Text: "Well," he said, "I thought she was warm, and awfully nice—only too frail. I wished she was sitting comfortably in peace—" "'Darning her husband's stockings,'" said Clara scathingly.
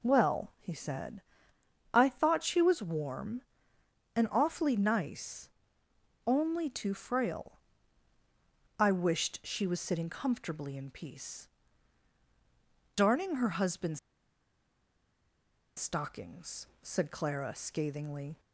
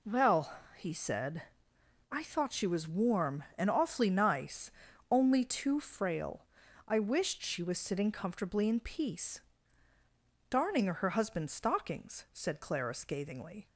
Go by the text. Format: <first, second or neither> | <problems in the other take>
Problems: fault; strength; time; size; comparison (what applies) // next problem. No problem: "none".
second | pauses between "husband's" and "stockings"; strong; at 13.9 s; 1.7 s long